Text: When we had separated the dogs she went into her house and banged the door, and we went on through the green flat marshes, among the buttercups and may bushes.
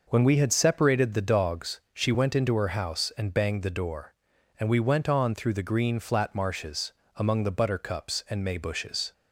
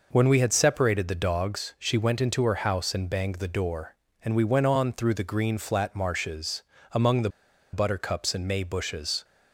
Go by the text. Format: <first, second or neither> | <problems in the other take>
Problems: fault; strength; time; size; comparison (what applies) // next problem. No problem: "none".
first | pauses between "the" and "buttercups"; at 7.2 s; 0.43 s long